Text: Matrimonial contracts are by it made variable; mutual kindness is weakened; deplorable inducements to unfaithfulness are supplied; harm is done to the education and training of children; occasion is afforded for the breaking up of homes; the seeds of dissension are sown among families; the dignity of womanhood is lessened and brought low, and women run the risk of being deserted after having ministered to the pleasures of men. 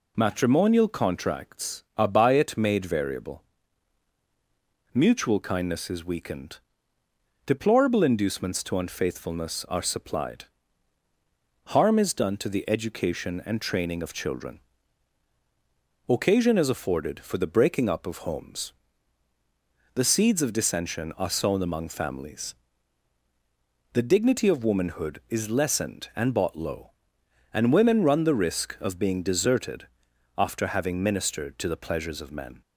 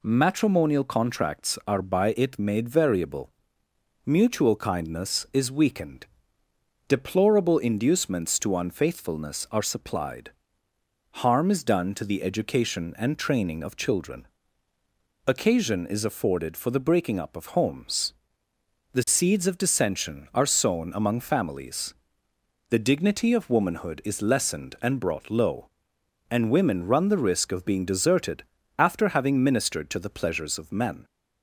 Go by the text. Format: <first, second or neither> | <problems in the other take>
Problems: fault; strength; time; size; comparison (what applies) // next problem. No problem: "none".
second | says "bought" for "brought"; at 26.3 s // pauses between "deserted" and "after"; noticeable; at 29.8 s; 0.52 s long; slight in the second